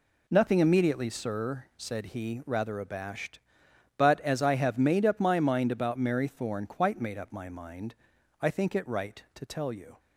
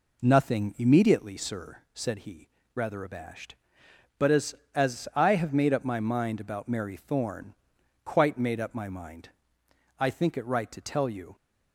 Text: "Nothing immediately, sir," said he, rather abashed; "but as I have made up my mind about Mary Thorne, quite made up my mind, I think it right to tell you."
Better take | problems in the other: first | says "as" twice; at 4.7 s

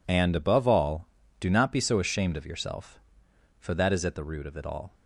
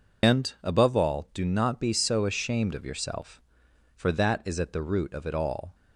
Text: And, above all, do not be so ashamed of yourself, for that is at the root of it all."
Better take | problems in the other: first | loses the start of "And"; at 0.2 s; 130 ms

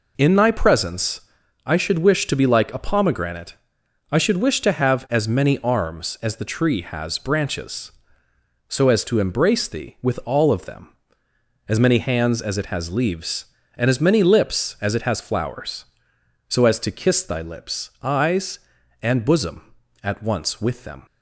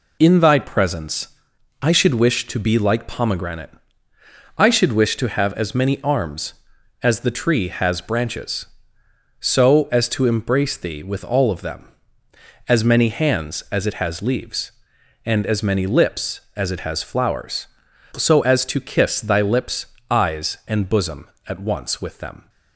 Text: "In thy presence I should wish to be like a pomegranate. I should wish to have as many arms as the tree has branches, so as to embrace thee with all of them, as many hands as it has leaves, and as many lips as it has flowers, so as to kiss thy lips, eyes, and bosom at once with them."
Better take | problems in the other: first | pauses between "presence" and "I"; noticeable; at 1.2 s; 0.54 s long; also in the first // skips "a"; at 3.0 s

